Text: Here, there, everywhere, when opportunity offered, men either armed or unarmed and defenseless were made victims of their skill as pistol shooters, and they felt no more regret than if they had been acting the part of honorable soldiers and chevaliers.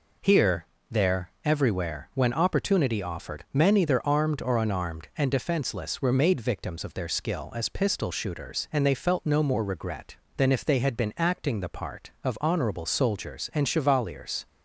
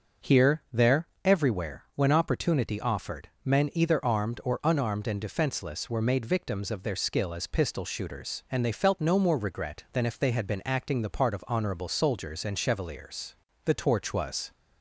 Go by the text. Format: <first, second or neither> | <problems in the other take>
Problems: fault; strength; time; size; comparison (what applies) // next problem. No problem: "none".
first | starts louder than the rest; noticeable; until 1.5 s; 6 dB // goes on to say "The torch was"; noticeable; from 13.6 s on; 0.88 s long